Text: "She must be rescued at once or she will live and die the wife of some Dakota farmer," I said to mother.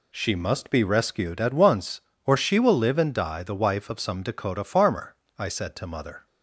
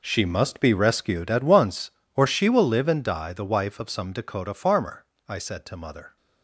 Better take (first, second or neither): first